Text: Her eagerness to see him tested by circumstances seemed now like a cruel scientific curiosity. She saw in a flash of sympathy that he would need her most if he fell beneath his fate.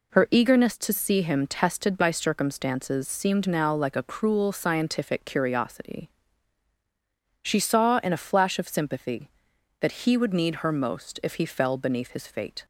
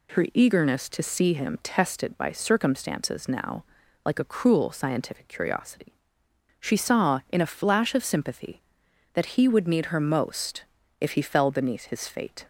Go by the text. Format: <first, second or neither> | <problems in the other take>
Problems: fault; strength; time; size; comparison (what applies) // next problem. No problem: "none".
first | skips "seemed"; at 3.2 s // pauses between "now" and "like"; at 3.6 s; 0.42 s long // pauses between "most" and "if"; slight; at 10.6 s; 0.34 s long